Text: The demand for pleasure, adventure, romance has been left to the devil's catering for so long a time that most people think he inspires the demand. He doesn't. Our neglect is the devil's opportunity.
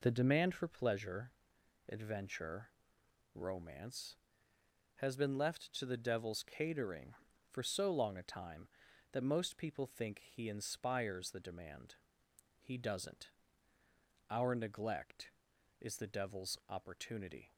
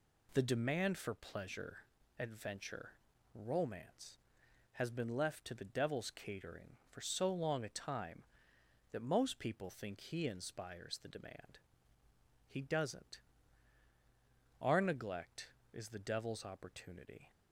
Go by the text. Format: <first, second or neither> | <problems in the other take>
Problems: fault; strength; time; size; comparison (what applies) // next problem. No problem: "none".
neither | none